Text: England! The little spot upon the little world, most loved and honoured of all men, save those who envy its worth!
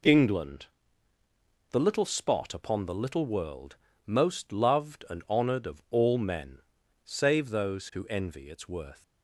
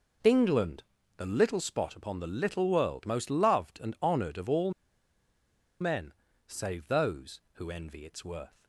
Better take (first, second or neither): first